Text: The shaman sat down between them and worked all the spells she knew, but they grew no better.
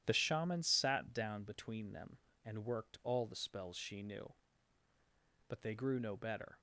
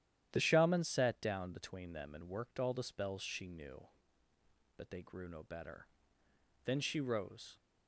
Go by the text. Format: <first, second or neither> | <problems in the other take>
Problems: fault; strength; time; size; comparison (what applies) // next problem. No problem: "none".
first | starts louder than the rest; strong; until 1.3 s; 11 dB; strong in the first // goes on to say "Then she rose"; noticeable; from 6.6 s on; 0.92 s long